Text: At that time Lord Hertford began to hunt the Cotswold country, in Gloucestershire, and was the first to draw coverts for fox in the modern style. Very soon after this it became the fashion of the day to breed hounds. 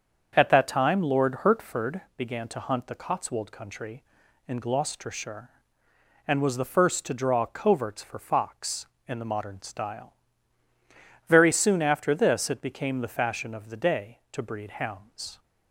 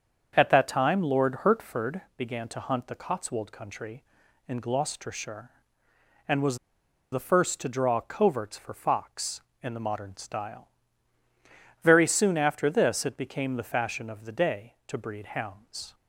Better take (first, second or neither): first